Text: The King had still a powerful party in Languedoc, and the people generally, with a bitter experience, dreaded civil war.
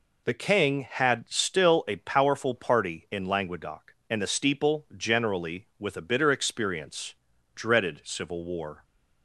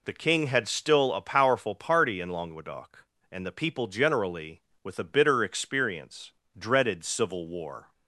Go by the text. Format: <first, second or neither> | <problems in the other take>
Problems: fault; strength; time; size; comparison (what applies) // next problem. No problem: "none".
second | says "steeple" for "people"; at 4.2 s